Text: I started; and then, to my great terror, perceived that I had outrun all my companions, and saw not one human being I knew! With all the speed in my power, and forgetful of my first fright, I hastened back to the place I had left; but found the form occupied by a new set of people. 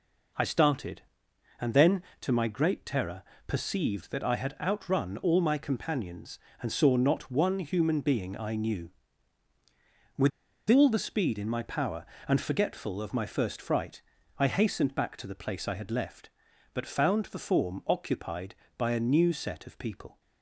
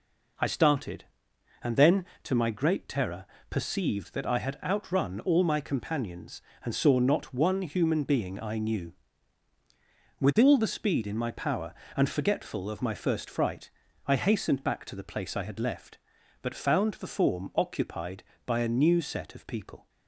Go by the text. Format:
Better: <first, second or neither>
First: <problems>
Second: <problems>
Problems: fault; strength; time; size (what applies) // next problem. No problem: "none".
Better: second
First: pauses between "With" and "all"; at 10.3 s; 0.39 s long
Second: none